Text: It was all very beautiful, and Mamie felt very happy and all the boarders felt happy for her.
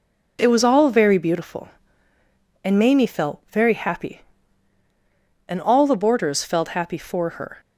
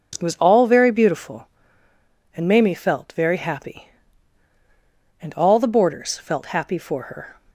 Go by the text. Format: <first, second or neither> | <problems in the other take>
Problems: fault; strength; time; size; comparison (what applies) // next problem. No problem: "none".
neither | none